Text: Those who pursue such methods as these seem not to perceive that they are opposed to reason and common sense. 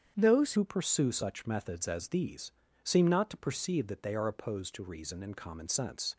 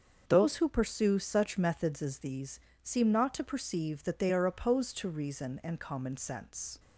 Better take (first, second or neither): second